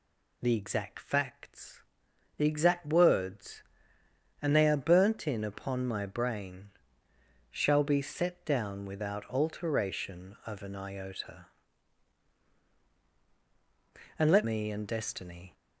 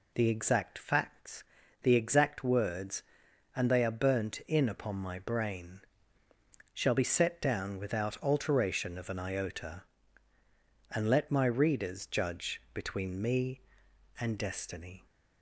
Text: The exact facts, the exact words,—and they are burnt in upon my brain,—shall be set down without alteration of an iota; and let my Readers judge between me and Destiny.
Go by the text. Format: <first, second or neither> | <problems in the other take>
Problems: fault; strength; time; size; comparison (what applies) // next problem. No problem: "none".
second | skips "my Readers judge between"; at 14.4 s